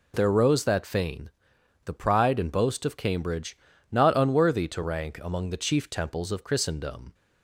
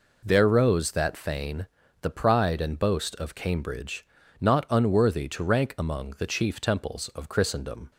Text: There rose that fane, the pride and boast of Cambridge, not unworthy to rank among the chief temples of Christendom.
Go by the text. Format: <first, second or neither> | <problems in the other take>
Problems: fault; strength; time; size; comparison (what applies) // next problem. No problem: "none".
neither | none